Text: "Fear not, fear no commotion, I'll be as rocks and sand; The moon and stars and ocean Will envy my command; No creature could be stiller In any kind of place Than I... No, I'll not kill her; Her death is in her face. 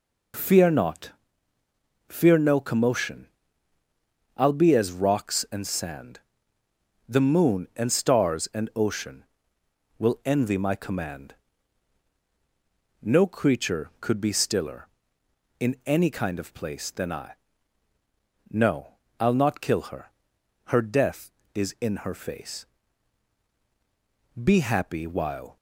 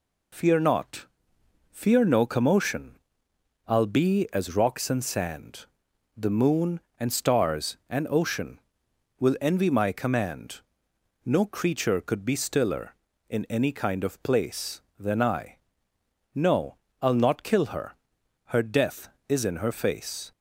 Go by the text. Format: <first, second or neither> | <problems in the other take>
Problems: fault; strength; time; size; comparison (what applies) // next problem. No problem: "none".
second | goes on to say "Be happy while"; noticeable; from 24.3 s on; 1.2 s long